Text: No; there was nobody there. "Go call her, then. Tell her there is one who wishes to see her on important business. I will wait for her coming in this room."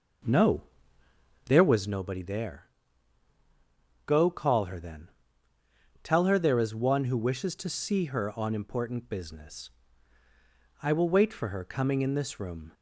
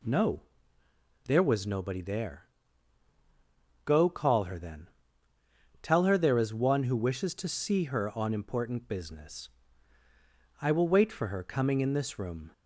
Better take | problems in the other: second | starts louder than the rest; noticeable; until 2.0 s; 6 dB

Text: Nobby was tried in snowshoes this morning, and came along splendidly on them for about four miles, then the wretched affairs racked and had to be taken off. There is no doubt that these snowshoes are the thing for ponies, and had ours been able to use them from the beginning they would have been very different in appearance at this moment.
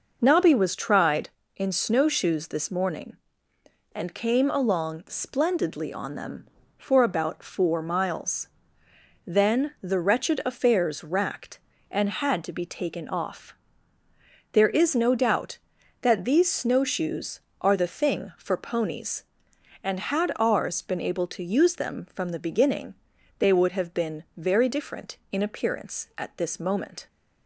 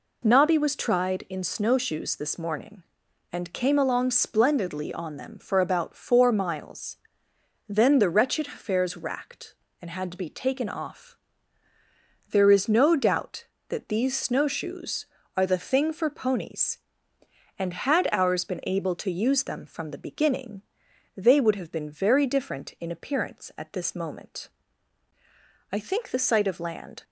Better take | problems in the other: first | pauses between "beginning" and "they"; noticeable; at 20.6 s; 0.54 s long; noticeable in the first // goes on to say "I think the sight of land"; from 25.7 s on; 1.3 s long

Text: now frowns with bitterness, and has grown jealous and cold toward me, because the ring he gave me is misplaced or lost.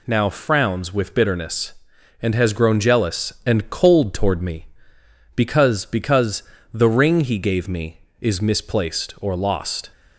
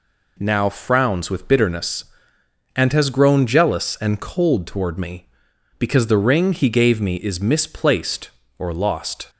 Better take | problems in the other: second | says "because" twice; at 5.8 s

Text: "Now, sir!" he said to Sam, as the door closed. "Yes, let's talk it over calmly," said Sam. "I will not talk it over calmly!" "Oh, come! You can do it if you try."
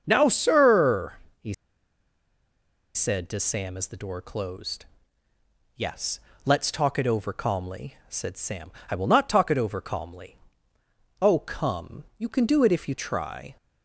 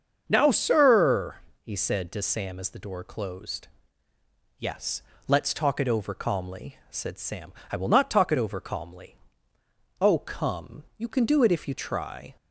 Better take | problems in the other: second | starts louder than the rest; until 1.0 s; 7 dB; also in the second // pauses between "he" and "said"; strong; at 1.5 s; 1.4 s long

